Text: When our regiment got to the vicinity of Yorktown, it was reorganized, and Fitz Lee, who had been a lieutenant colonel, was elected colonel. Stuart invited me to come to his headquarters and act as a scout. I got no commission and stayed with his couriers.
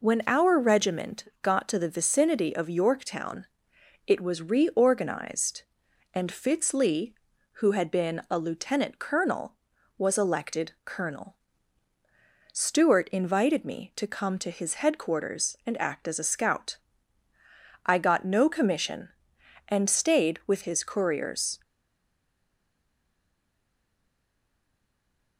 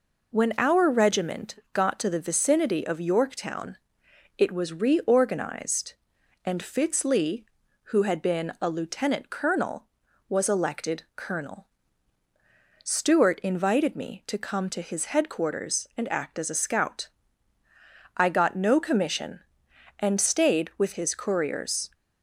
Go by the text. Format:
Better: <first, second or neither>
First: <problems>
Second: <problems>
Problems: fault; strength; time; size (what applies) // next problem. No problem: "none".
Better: second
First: pauses between "regiment" and "got"; slight; at 1.2 s; 0.18 s long // stays silent after the last word; strong; from 21.6 s on; 3.7 s long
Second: pauses between "regiment" and "got"; slight; at 1.5 s; 0.18 s long